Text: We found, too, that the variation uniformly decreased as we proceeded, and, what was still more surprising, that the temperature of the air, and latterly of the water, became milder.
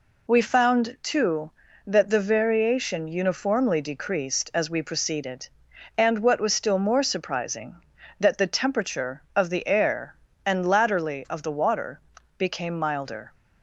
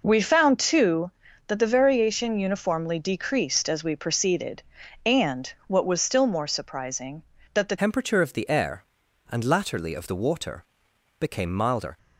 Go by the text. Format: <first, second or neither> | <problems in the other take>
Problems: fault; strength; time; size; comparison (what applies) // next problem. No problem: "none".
first | changes voice at "temperature"; from 7.7 s on; 4.2 s long